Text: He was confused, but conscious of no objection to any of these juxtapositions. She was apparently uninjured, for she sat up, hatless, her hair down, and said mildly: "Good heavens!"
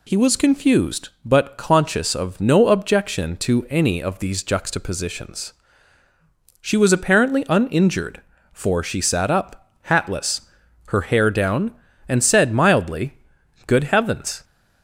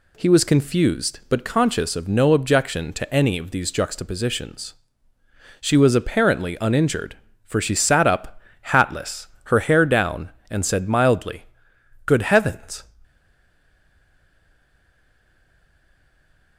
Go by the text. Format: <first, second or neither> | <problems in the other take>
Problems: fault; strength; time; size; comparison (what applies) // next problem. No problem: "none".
first | stays silent after the last word; strong; from 13.0 s on; 3.5 s long